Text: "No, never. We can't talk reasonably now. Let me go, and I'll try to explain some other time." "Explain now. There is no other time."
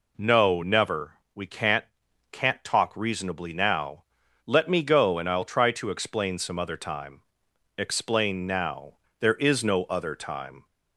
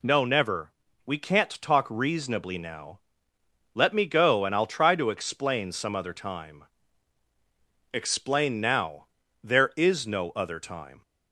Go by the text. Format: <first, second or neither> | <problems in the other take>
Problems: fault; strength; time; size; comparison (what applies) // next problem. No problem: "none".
second | says "can't" twice; at 2.3 s